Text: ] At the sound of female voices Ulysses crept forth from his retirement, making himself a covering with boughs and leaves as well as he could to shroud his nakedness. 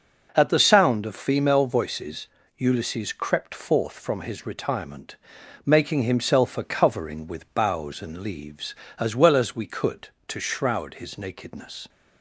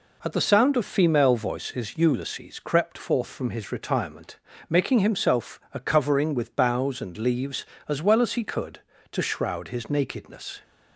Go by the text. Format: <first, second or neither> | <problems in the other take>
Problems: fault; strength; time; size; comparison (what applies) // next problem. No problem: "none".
second | pauses between "voices" and "Ulysses"; slight; at 2.2 s; 0.28 s long // says "we" for "he"; at 9.5 s